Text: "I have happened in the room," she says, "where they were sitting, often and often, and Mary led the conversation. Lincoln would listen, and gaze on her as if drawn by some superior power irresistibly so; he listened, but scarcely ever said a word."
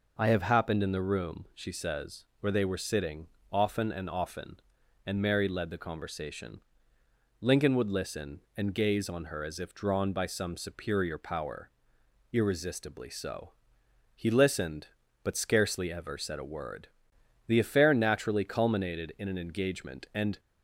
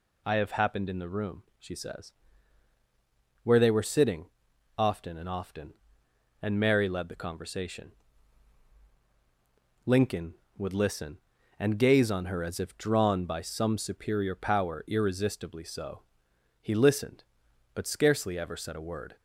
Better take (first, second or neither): second